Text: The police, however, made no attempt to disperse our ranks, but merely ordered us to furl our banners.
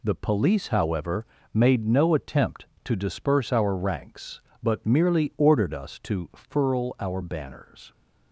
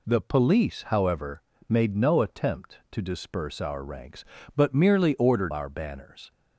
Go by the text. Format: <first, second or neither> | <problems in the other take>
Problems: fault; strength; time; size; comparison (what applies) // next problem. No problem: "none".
first | skips "us to furl"; at 5.5 s